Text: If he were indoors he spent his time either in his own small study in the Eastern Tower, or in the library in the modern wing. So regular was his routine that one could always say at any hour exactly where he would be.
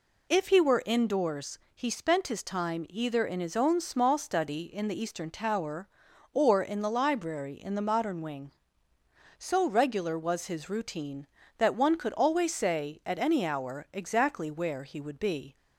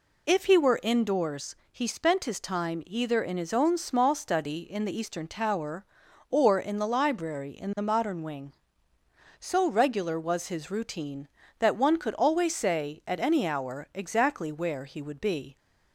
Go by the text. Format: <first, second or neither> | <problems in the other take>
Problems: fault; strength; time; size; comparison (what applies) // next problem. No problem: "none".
neither | pauses between "indoors" and "he"; slight; the same in both